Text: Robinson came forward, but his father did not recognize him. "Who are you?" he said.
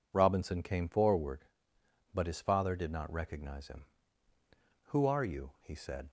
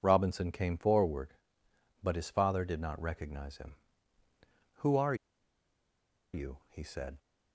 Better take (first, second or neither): first